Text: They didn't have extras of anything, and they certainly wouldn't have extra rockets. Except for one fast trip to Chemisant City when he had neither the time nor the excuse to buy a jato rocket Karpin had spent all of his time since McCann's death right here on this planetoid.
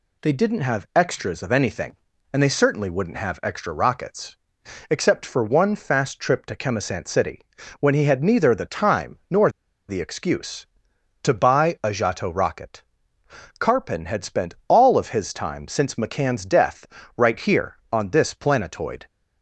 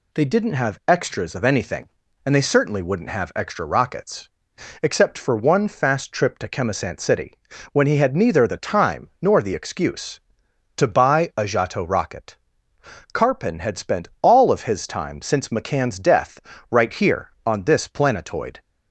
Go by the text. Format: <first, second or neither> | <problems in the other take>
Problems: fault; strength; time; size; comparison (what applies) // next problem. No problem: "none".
second | pauses between "City" and "when"; at 7.3 s; 0.40 s long; also in the second // pauses between "nor" and "the"; at 9.4 s; 0.39 s long // pauses between "rocket" and "Karpin"; noticeable; at 12.8 s; 0.78 s long; noticeable in the second // pauses between "death" and "right"; slight; at 16.8 s; 0.32 s long; slight in the second